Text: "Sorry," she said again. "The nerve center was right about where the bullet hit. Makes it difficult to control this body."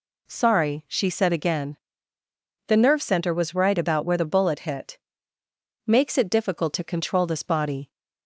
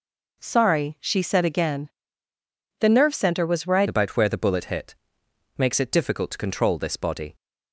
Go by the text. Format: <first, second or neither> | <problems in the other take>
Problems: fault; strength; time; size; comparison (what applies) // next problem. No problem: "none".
first | changes voice at "about"; from 3.8 s on; 3.5 s long